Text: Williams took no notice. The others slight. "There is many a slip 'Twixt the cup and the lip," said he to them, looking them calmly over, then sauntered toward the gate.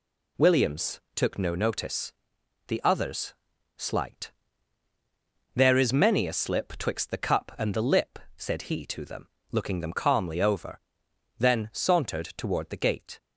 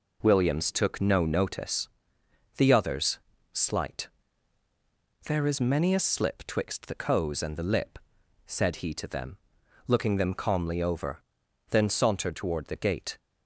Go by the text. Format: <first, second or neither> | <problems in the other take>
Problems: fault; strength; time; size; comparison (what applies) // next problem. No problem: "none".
first | pauses between "others" and "slight"; slight; at 3.1 s; 0.34 s long; also in the first // says "coes" for "cup"; at 6.9 s